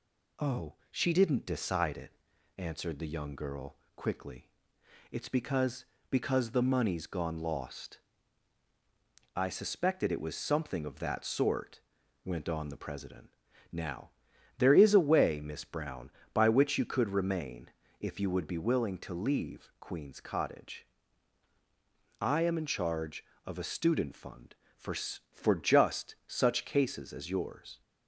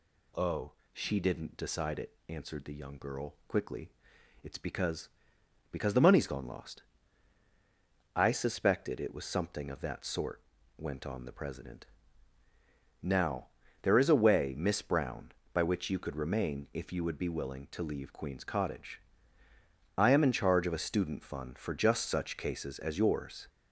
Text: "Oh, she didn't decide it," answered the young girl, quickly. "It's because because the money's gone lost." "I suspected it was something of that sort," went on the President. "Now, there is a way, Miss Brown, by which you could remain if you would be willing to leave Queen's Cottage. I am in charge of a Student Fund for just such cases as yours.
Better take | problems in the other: second | pauses between "remain" and "if"; slight; at 17.6 s; 0.32 s long // says "for" twice; at 24.9 s

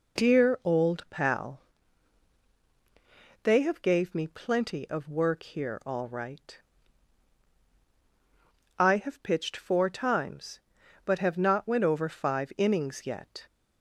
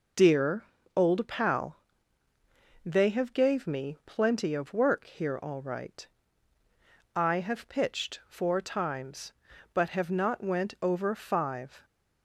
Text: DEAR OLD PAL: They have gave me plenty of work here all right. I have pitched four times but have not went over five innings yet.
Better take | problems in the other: first | pauses between "DEAR" and "OLD"; slight; at 0.6 s; 0.32 s long // stops before "innings yet"; at 11.8 s

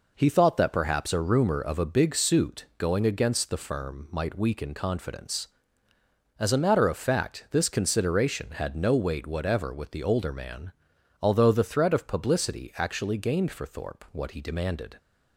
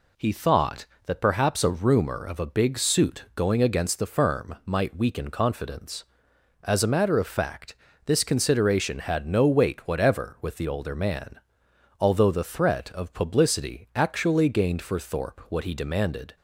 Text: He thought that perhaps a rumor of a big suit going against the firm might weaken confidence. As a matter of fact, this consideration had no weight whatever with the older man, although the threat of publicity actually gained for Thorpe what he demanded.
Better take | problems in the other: neither | none

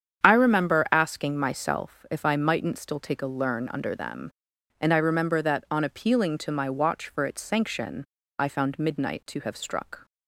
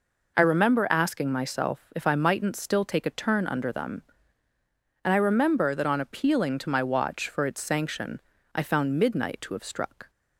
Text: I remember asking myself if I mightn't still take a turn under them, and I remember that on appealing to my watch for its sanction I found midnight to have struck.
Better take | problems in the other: second | starts louder than the rest; strong; until 1.2 s; 8.5 dB // says "learn" for "turn"; at 3.2 s // pauses between "sanction" and "I"; slight; at 8.0 s; 0.32 s long; slight in the second

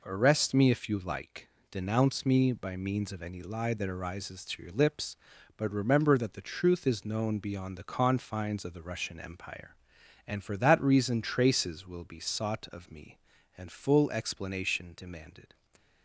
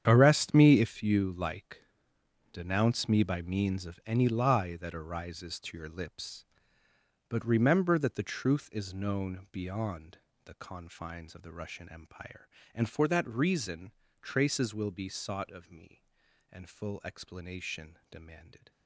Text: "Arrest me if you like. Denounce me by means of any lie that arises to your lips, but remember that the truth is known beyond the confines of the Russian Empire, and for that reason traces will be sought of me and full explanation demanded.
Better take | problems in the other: first | gets quieter; strong; throughout; 14 dB // pauses between "beyond" and "the"; slight; at 10.1 s; 0.26 s long // pauses between "reason" and "traces"; slight; at 13.9 s; 0.32 s long

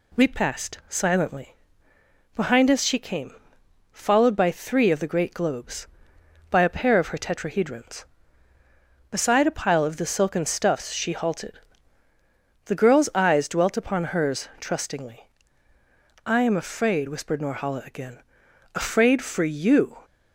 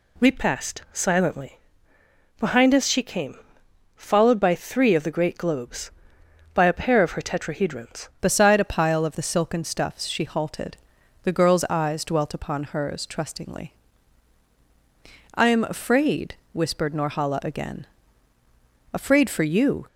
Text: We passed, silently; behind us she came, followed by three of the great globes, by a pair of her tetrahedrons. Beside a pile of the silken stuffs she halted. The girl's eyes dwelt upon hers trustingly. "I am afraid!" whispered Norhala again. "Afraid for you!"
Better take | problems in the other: first | changes voice at "Beside"; from 8.2 s on; 11.6 s long

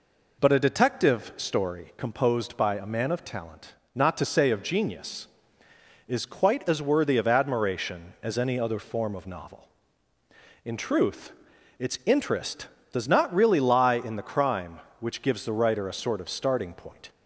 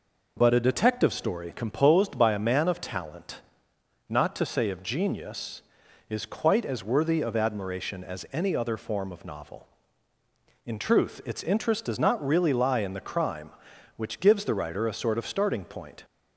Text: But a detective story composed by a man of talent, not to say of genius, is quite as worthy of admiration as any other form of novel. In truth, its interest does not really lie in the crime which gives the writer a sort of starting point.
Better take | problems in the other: neither | none

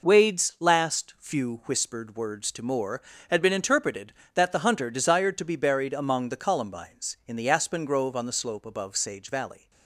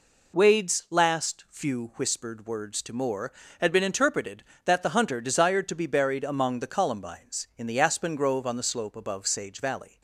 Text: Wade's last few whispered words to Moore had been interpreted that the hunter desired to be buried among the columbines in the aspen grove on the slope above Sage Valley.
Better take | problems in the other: second | gets quieter; throughout; 6.5 dB

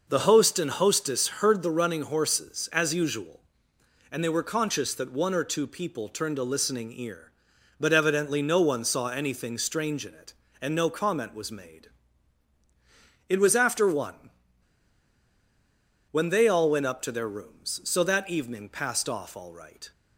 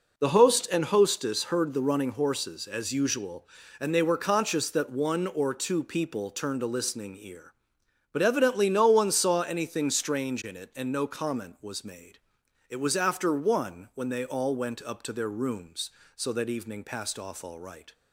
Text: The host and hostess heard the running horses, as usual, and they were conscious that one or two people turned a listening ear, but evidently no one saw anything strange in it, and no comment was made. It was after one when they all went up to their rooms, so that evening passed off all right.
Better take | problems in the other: second | pauses between "one" and "when"; strong; at 14.3 s; 1.8 s long

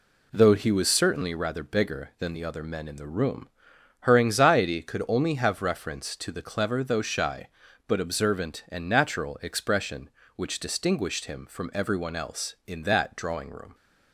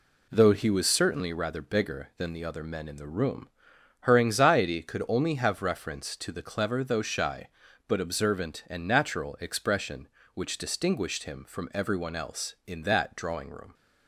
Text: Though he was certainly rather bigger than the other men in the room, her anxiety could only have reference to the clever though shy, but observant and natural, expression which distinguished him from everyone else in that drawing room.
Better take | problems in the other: neither | none

